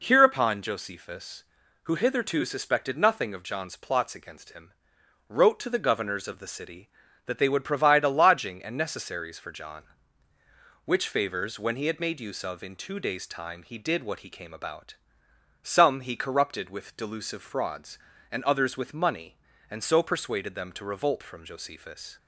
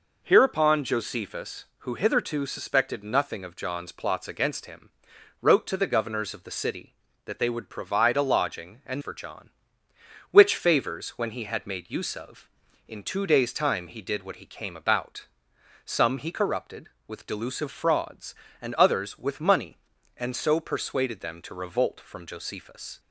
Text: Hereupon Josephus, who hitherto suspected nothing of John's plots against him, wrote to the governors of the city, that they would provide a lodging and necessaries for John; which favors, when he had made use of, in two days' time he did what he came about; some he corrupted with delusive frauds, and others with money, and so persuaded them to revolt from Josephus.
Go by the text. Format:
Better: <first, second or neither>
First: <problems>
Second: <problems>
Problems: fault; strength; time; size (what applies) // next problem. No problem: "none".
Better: first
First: none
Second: skips "necessaries"; at 9.0 s